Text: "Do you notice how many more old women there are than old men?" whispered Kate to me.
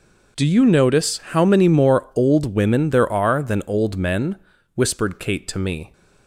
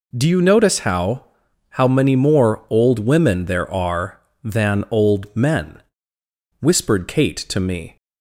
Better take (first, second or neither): first